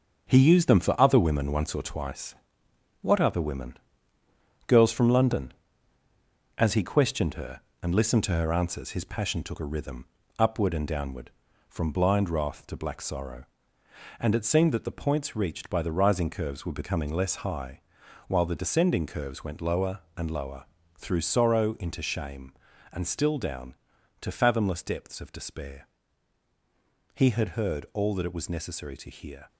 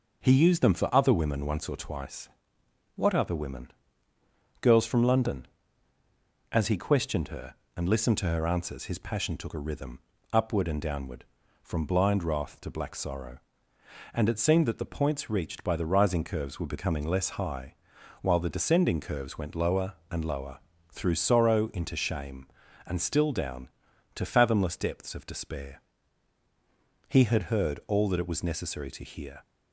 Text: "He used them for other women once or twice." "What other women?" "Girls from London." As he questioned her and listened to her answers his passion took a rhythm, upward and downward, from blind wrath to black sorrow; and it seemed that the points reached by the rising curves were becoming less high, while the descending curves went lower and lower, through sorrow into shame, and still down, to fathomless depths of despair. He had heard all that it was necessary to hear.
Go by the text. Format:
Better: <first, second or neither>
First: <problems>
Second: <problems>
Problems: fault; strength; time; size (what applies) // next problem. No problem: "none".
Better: second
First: gets quieter; throughout; 6.5 dB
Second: none